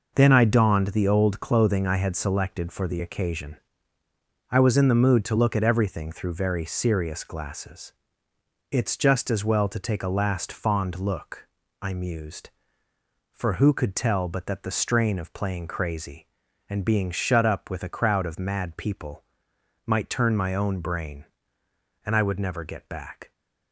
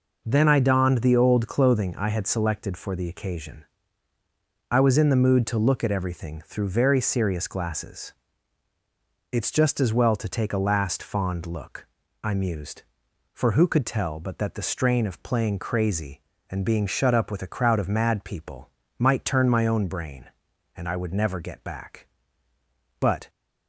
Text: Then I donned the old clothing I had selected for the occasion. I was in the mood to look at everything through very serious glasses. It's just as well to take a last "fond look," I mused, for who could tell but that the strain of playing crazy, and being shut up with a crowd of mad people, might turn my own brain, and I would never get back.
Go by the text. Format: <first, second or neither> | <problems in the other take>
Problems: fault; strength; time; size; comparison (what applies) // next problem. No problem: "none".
first | goes on to say "But"; slight; from 22.9 s on; 0.30 s long